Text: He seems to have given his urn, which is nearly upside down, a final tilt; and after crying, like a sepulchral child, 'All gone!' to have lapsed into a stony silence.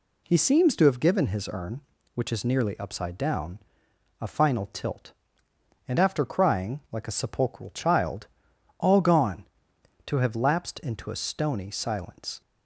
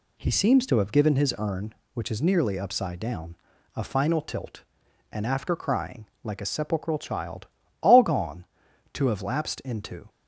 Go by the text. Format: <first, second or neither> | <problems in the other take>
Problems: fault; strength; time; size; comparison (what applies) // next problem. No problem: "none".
first | stops before "a stony silence"; at 10.0 s